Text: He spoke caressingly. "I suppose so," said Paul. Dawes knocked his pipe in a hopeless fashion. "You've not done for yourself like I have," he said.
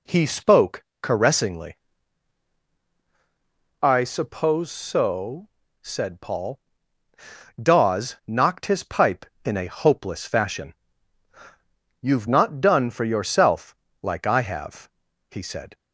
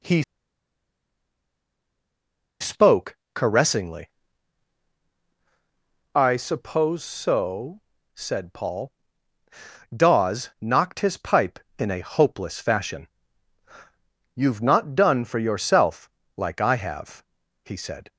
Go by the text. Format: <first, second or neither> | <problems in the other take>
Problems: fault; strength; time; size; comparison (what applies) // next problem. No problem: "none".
first | pauses between "He" and "spoke"; strong; at 0.2 s; 2.3 s long // pauses between "spoke" and "caressingly"; slight; at 3.1 s; 0.18 s long; slight in the first // pauses between "yourself" and "like"; slight; at 16.1 s; 0.24 s long; slight in the first